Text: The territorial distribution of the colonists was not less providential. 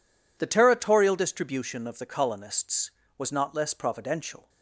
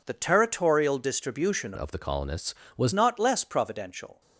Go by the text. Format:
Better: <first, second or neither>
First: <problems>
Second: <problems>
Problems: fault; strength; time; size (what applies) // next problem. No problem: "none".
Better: first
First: none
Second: changes voice from "of" to "was"; from 1.7 to 2.9 s; 1.2 s long